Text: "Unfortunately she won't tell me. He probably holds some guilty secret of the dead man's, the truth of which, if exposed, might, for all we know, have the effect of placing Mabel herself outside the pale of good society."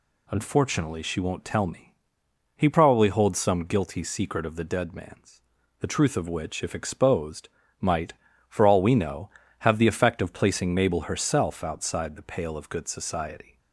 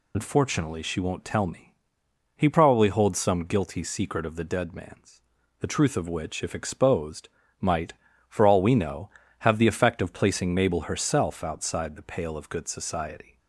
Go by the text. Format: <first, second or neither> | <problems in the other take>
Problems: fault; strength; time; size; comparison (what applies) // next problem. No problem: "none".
first | loses the start of "Unfortunately"; at 0.1 s; 60 ms